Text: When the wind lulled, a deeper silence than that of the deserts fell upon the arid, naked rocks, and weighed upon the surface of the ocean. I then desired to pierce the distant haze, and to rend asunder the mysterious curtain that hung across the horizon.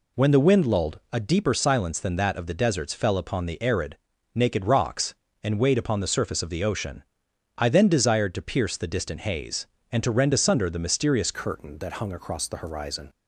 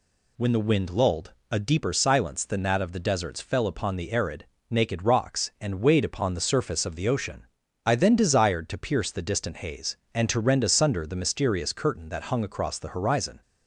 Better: second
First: changes voice at "curtain"; from 11.3 s on; 1.7 s long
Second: none

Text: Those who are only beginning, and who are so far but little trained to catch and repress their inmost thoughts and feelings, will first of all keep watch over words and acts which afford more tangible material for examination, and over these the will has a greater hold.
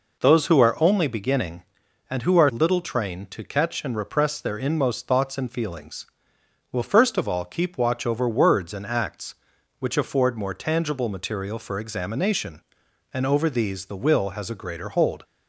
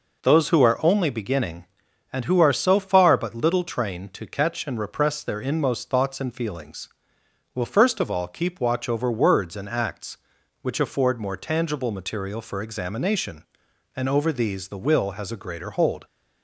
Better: second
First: skips "so far but"; at 2.5 s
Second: none

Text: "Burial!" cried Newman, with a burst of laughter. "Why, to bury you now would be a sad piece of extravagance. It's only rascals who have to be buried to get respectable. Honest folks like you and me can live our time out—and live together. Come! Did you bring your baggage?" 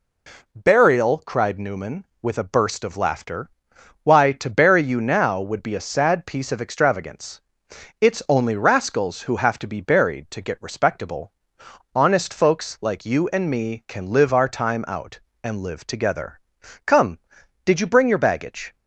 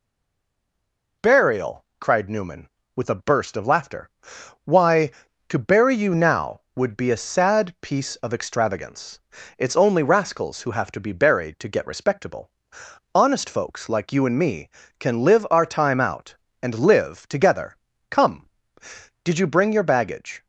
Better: first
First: none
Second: stays silent before the first word; noticeable; until 1.2 s; 1.2 s long

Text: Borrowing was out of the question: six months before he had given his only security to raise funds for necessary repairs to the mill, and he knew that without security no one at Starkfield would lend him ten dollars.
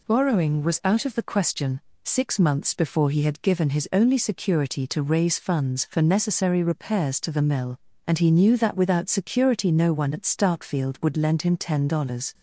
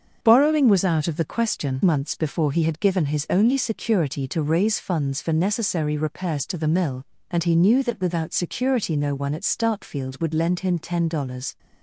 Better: first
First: none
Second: starts louder than the rest; strong; until 1.2 s; 7 dB // skips "six"; at 1.8 s

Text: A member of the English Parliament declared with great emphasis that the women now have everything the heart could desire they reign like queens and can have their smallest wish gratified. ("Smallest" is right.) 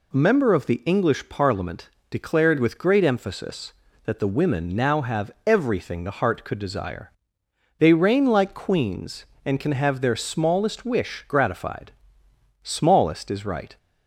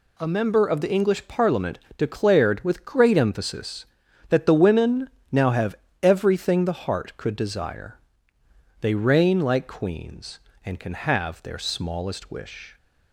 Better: first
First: pauses between "Parliament" and "declared"; slight; at 1.8 s; 0.22 s long // pauses between "have" and "everything"; slight; at 5.3 s; 0.16 s long // pauses between "desire" and "they"; noticeable; at 7.1 s; 0.66 s long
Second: pauses between "Parliament" and "declared"; slight; at 1.7 s; 0.20 s long // pauses between "women" and "now"; slight; at 5.1 s; 0.20 s long // pauses between "have" and "everything"; slight; at 5.7 s; 0.26 s long // pauses between "desire" and "they"; noticeable; at 7.9 s; 0.82 s long // stops before "gratified Smallest is right"; at 12.7 s

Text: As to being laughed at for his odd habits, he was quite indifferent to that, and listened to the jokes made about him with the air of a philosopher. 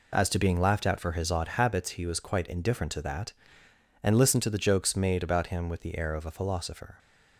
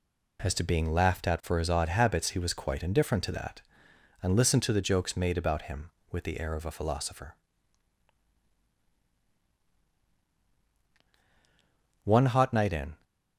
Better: first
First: none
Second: goes on to say "One hot night in"; noticeable; from 12.0 s on; 0.98 s long

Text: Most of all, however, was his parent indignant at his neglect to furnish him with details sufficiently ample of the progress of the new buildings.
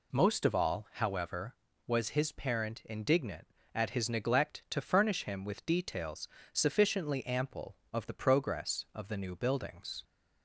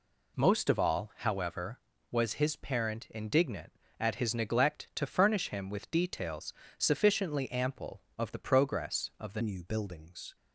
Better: first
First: pauses between "details" and "sufficiently"; slight; at 6.2 s; 0.24 s long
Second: pauses between "details" and "sufficiently"; slight; at 6.5 s; 0.24 s long // changes voice at "new"; from 9.4 s on; 0.9 s long

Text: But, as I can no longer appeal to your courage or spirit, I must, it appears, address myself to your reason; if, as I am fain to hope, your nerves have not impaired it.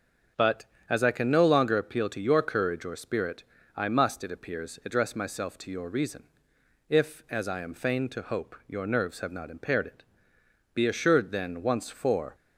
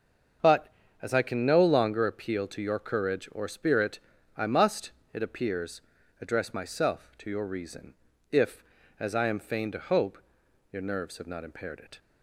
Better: second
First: starts louder than the rest; until 1.6 s; 7 dB // goes on to say "Be assured then once for"; from 10.7 s on; 1.6 s long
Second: starts louder than the rest; until 1.7 s; 6.5 dB

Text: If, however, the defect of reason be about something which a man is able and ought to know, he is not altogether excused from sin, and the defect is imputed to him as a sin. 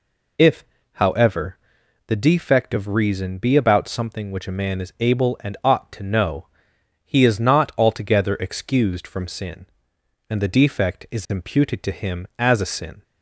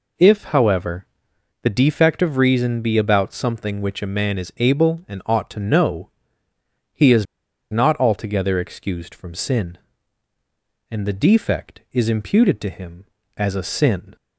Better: first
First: none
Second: pauses between "is" and "not"; noticeable; at 7.2 s; 0.46 s long

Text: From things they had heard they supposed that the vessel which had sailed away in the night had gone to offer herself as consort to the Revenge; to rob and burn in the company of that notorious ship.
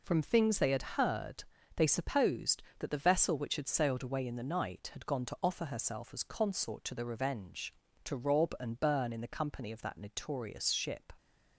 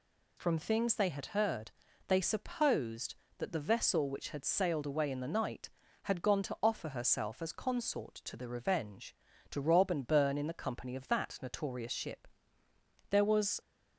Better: first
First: pauses between "heard" and "they"; slight; at 1.4 s; 0.32 s long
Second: pauses between "heard" and "they"; slight; at 1.7 s; 0.34 s long // goes on to say "There was"; from 13.1 s on; 0.50 s long

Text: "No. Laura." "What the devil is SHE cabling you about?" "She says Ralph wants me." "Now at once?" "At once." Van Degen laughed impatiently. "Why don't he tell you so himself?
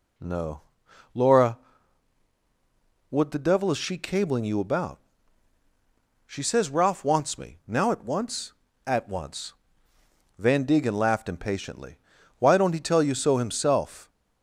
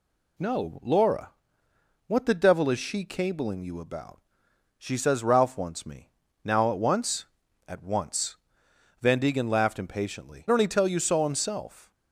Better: first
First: none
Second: skips "Why"; at 10.4 s

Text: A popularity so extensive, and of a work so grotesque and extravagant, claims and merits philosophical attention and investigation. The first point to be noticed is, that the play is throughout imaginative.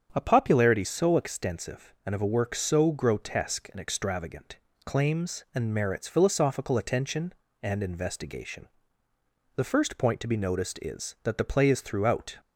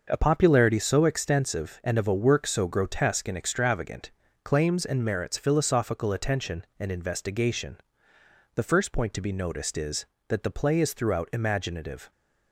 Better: second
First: starts louder than the rest; strong; until 1.1 s; 7.5 dB // stops before "imaginative"; at 12.3 s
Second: starts louder than the rest; until 1.1 s; 6 dB

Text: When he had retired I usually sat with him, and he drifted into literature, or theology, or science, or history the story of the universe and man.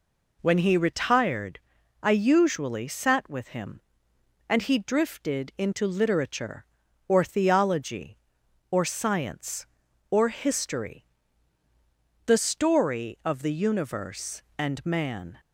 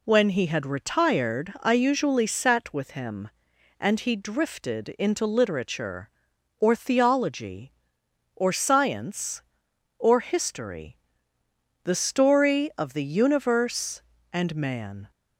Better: second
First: skips "had"; at 0.7 s // pauses between "retired" and "I"; at 1.5 s; 0.42 s long // pauses between "history" and "the"; at 11.0 s; 1.2 s long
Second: pauses between "history" and "the"; noticeable; at 10.9 s; 0.88 s long

